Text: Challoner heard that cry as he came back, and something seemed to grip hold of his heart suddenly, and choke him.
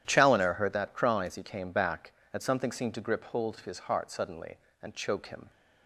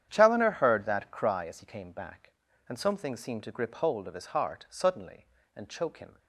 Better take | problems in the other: neither | starts louder than the rest; strong; the same in both

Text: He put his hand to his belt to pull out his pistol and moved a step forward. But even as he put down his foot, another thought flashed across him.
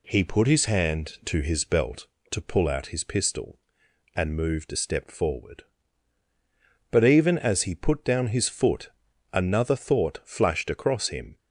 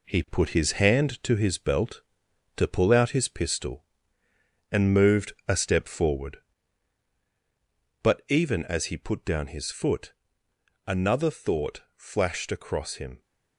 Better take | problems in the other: first | gets quieter; noticeable; throughout; 5.5 dB

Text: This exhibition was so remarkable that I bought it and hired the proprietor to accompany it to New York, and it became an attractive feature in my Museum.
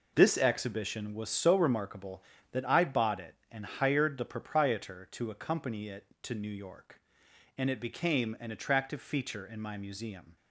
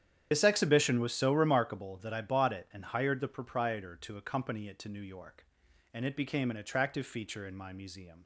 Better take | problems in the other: first | loses the start of "This"; at 0.3 s; 60 ms // starts louder than the rest; strong; until 1.3 s; 9.5 dB

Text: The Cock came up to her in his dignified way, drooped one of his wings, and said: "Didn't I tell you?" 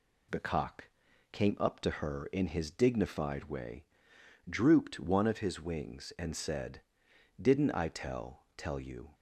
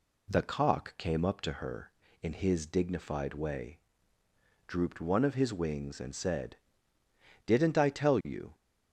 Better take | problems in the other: second | pauses between "Cock" and "came"; at 0.8 s; 0.42 s long // says "tell" twice; at 8.5 s

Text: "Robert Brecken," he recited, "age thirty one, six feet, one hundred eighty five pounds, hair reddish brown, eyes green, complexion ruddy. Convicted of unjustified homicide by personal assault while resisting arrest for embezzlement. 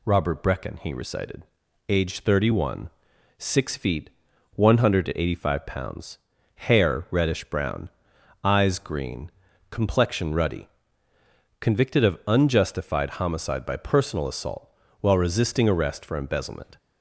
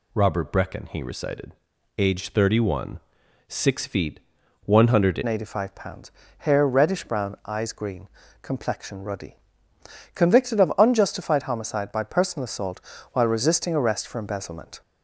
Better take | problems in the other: first | changes voice at "eighty"; from 5.2 s on; 9.6 s long // pauses between "assault" and "while"; slight; at 12.8 s; 0.32 s long; slight in the first

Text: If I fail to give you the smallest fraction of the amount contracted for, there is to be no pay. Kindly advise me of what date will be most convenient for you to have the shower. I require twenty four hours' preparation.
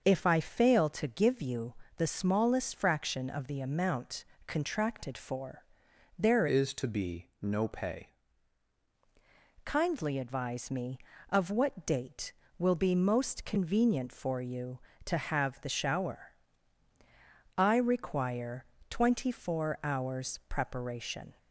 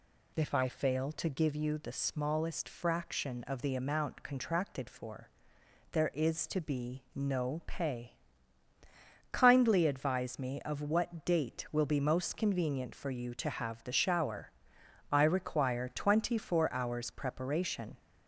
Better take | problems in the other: second | starts louder than the rest; until 1.0 s; 6.5 dB // pauses between "you" and "the"; slight; at 1.7 s; 0.24 s long // pauses between "amount" and "contracted"; slight; at 4.2 s; 0.22 s long // changes voice from "is" to "pay"; from 6.4 to 8.1 s; 1.7 s long // pauses between "require" and "twenty"; slight; at 18.6 s; 0.26 s long

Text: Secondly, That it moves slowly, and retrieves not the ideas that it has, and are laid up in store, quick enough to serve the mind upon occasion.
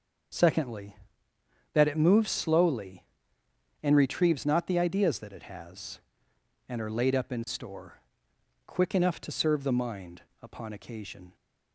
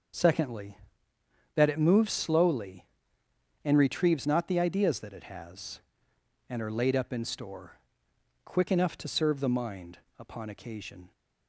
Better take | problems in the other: neither | starts louder than the rest; the same in both // pauses between "mind" and "upon"; slight; the same in both

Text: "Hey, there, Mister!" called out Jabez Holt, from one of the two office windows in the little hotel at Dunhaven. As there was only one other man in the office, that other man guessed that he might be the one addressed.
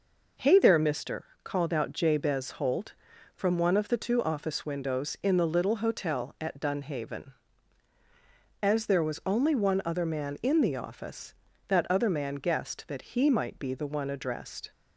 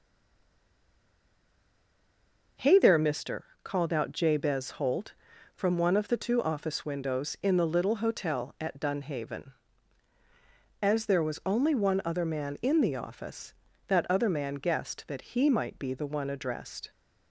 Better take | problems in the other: first | stays silent before the first word; strong; until 2.5 s; 2.5 s long

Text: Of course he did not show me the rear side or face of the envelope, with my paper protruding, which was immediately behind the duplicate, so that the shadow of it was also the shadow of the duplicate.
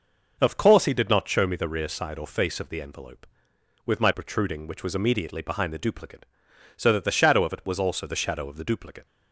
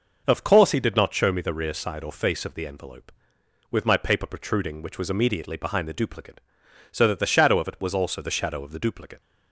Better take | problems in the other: second | skips "paper"; at 4.1 s

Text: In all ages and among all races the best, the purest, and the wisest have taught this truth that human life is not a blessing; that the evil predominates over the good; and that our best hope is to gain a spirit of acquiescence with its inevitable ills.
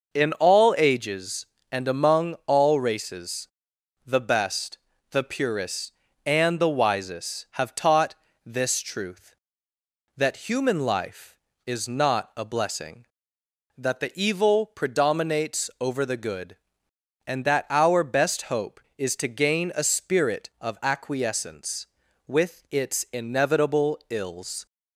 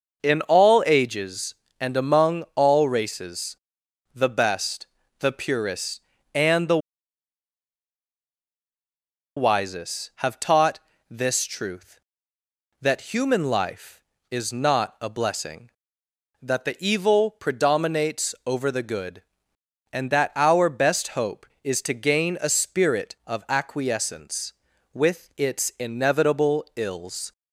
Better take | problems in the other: first | pauses between "races" and "the"; noticeable; at 3.5 s; 0.58 s long; noticeable in the first // pauses between "the" and "wisest"; strong; at 6.7 s; 2.5 s long // pauses between "taught" and "this"; slight; at 10.7 s; 0.30 s long; slight in the first

